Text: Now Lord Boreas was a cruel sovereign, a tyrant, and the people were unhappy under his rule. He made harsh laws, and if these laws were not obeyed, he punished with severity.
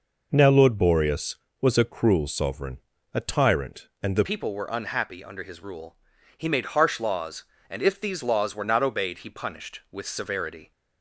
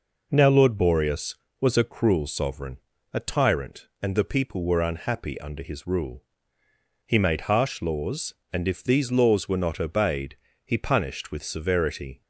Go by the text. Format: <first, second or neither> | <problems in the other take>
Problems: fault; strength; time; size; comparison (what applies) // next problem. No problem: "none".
second | changes voice at "people"; from 4.2 s on; 6.5 s long